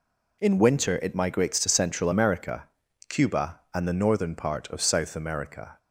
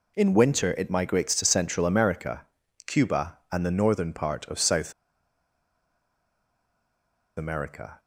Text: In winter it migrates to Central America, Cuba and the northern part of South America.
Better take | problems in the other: first | pauses between "South" and "America"; strong; at 4.9 s; 2.4 s long

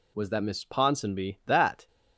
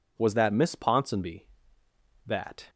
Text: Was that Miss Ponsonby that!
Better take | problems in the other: neither | none

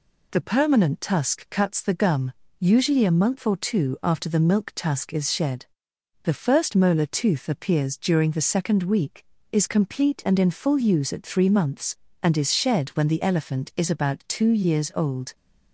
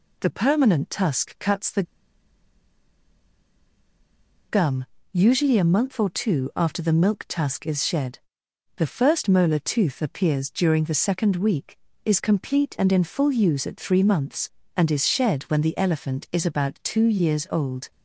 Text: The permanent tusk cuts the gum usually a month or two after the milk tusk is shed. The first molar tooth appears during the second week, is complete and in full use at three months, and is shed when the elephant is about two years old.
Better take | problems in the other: first | pauses between "the" and "gum"; strong; at 1.8 s; 2.6 s long // pauses between "gum" and "usually"; slight; at 4.8 s; 0.26 s long; slight in the first

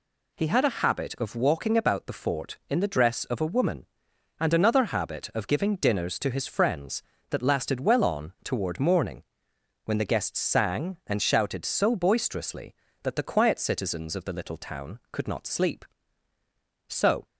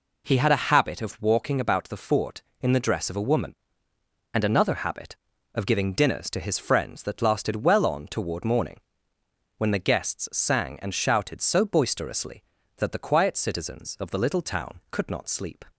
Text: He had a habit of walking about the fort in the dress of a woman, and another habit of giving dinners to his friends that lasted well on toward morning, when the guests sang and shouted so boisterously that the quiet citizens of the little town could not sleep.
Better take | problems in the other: second | goes on to say "So"; slight; from 16.8 s on; 0.38 s long

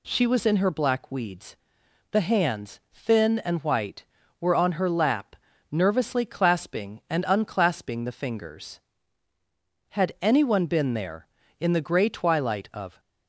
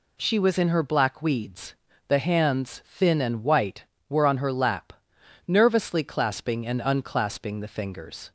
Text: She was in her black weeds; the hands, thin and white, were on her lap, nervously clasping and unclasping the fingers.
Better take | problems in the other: second | goes on to say "Had anyone been there in the grey twilight of"; strong; from 9.8 s on; 3.1 s long

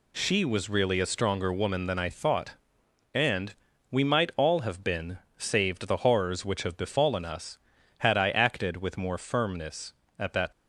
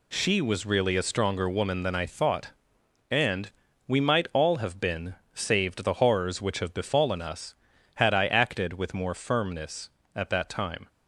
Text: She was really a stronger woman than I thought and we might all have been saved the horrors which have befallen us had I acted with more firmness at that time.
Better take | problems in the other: second | pauses between "and" and "we"; at 3.5 s; 0.38 s long; also in the second // pauses between "been" and "saved"; slight; at 5.1 s; 0.20 s long; slight in the second // stops before "time"; at 10.5 s

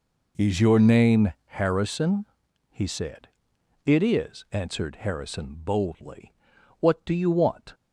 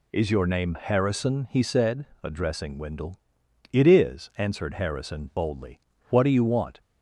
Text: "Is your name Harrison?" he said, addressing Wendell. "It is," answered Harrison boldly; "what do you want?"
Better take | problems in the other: second | skips "addressing Wendell"; at 3.5 s

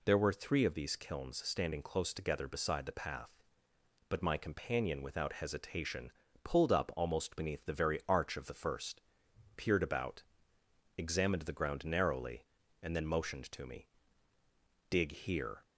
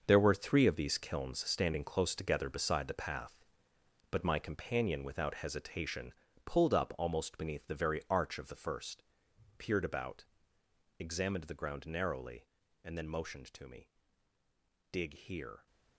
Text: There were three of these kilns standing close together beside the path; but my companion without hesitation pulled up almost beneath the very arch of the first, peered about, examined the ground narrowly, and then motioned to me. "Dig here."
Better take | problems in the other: first | gets quieter; strong; throughout; 11.5 dB // pauses between "hesitation" and "pulled"; slight; at 6.1 s; 0.32 s long; slight in the first

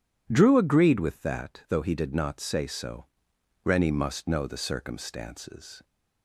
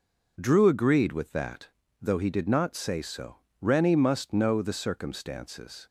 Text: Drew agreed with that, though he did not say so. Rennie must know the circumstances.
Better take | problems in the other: neither | none

